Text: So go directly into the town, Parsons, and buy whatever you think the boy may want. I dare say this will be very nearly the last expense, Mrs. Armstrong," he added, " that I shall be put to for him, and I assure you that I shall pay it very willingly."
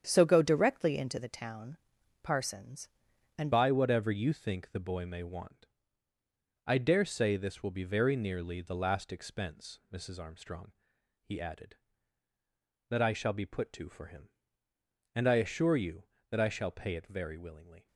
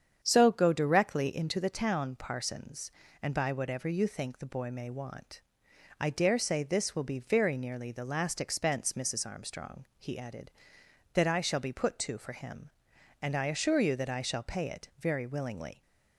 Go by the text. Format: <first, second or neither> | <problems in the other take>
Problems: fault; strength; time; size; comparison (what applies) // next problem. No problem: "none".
second | starts louder than the rest; strong; until 1.0 s; 8.5 dB; strong in the second // changes voice at "buy"; from 3.5 s on; 14.3 s long